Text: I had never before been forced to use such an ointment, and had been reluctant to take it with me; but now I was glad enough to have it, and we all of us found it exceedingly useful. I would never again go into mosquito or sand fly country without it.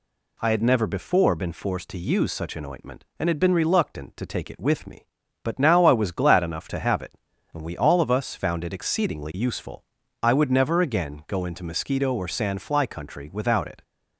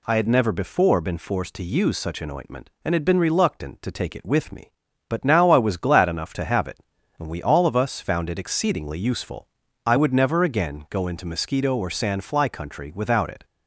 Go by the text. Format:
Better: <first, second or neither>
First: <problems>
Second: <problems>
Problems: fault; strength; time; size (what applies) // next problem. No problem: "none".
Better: neither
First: none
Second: none